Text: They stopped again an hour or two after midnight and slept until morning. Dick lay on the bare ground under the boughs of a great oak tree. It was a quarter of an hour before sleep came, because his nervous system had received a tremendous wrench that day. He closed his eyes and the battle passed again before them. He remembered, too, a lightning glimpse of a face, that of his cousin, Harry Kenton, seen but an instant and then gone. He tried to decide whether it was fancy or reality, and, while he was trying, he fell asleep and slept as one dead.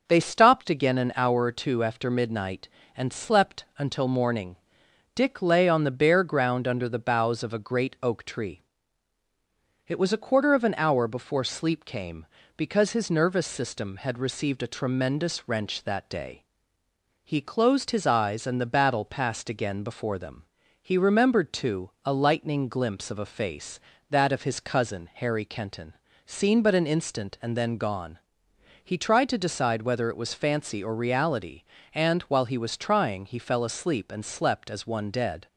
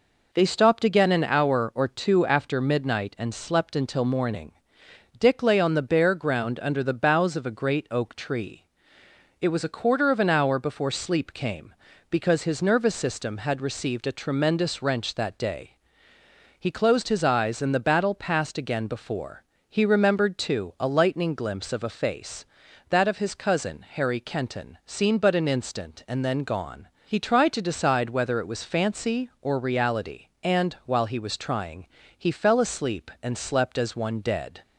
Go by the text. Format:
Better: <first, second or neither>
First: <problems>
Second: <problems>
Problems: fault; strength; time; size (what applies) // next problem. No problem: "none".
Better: first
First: none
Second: skips "them"; at 19.5 s